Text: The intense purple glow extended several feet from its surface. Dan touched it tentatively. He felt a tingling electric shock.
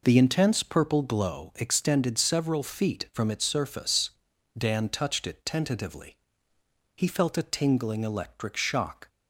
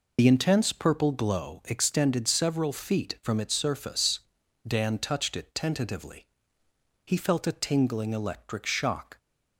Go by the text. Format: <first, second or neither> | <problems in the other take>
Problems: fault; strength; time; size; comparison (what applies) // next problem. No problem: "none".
first | loses the start of "The"; at 0.1 s; 60 ms